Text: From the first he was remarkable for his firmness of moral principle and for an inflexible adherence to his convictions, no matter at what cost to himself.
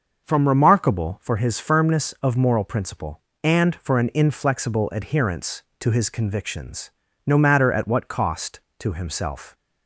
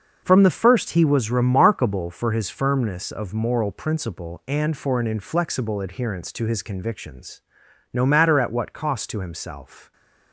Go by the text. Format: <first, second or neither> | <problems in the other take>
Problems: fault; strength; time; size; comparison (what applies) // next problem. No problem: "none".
second | starts louder than the rest; noticeable; until 1.2 s; 6 dB; also in the second // skips "the first he was"; at 0.4 s